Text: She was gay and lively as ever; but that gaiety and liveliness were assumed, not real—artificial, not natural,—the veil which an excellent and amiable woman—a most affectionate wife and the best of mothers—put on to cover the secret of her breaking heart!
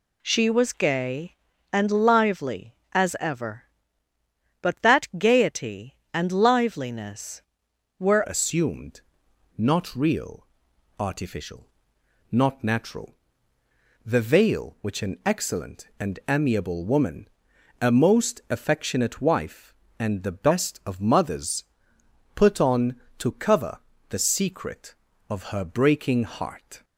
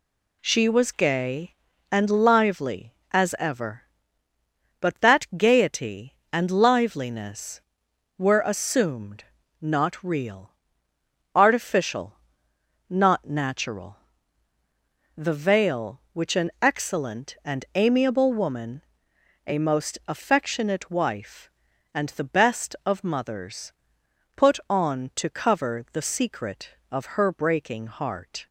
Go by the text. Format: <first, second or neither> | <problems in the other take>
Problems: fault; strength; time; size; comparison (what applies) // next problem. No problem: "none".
second | changes voice at "assumed"; from 8.2 s on; 18.6 s long // pauses between "cover" and "the"; slight; at 23.7 s; 0.30 s long